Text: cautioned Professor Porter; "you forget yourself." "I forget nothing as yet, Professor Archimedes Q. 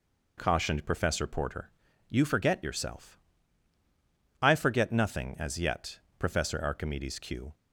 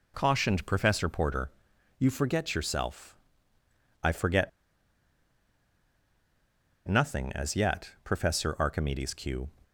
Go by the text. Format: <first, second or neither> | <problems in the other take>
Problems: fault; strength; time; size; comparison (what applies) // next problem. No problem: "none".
first | pauses between "forget" and "nothing"; strong; at 4.4 s; 2.3 s long